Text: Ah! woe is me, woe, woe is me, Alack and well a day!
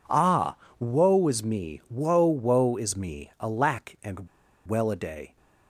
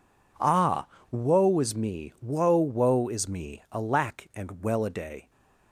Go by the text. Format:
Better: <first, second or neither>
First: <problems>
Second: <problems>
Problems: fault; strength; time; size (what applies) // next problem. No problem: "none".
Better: second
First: pauses between "and" and "well"; at 4.2 s; 0.40 s long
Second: none